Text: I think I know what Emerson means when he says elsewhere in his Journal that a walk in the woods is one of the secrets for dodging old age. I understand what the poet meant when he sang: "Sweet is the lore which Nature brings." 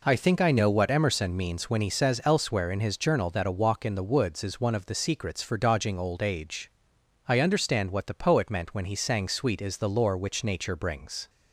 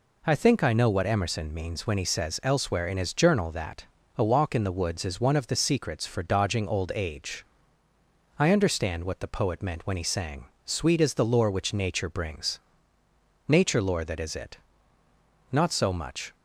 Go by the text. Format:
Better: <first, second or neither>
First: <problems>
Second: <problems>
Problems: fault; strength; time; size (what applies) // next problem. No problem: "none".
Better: first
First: none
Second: pauses between "that" and "a"; slight; at 3.8 s; 0.30 s long // goes on to say "Nature lore that is it Not so much"; strong; from 13.4 s on; 2.8 s long